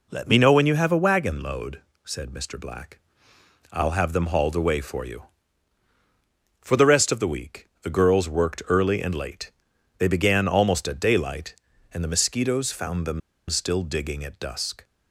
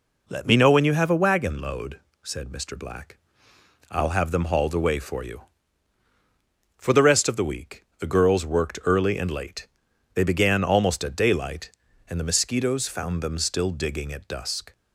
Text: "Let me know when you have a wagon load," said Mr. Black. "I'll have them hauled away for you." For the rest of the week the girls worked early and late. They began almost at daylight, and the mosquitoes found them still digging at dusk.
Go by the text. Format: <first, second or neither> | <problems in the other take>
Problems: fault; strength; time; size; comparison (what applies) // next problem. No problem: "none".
second | pauses between "them" and "still"; slight; at 13.2 s; 0.29 s long